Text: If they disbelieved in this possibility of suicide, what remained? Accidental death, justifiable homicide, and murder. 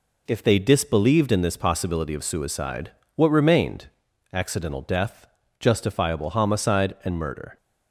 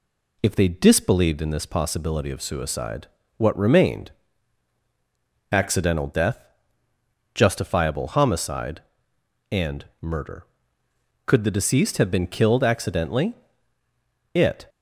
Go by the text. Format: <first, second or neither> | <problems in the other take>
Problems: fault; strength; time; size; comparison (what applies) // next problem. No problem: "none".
first | pauses between "and" and "murder"; slight; at 9.8 s; 0.16 s long // goes on to say "Could the deceased have been killed accidentally It"; strong; from 11.2 s on; 3.4 s long